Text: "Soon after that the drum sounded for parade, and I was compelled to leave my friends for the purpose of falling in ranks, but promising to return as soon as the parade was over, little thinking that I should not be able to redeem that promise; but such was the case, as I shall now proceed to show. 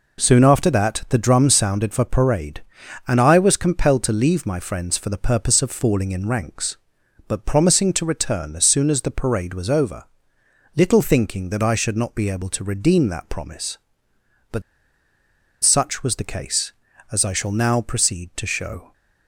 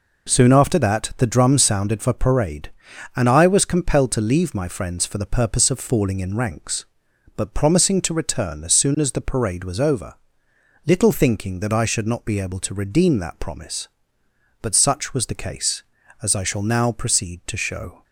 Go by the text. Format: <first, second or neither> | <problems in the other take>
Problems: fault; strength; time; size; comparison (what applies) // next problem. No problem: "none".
second | pauses between "but" and "such"; at 14.6 s; 1.0 s long